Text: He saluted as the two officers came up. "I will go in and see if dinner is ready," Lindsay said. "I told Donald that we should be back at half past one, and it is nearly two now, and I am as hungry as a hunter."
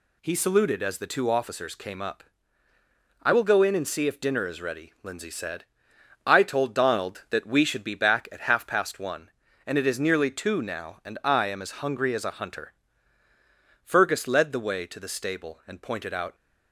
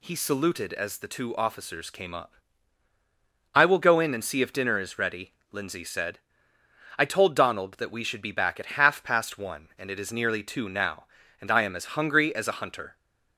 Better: second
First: goes on to say "Fergus led the way to the stable and pointed out"; strong; from 13.8 s on; 2.5 s long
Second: none

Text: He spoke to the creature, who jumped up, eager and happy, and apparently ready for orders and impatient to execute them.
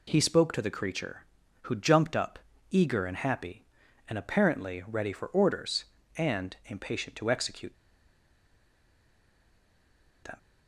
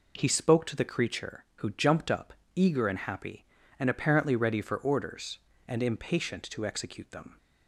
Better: second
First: pauses between "execute" and "them"; strong; at 7.7 s; 2.4 s long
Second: none

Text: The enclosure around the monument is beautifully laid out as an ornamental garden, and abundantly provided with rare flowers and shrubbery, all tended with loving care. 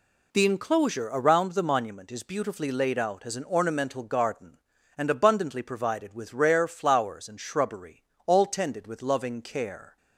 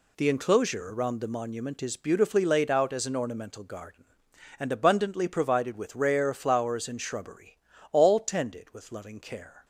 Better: neither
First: none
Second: none

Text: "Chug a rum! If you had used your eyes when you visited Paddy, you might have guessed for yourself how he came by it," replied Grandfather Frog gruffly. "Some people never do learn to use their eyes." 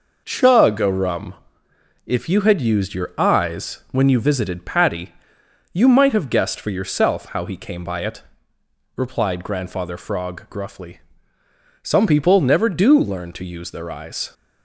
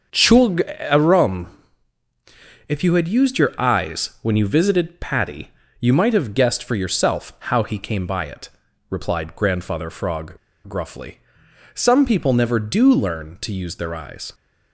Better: first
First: none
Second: starts louder than the rest; until 1.3 s; 7 dB // pauses between "Chug" and "a"; slight; at 0.6 s; 0.18 s long // pauses between "Frog" and "gruffly"; slight; at 10.3 s; 0.34 s long

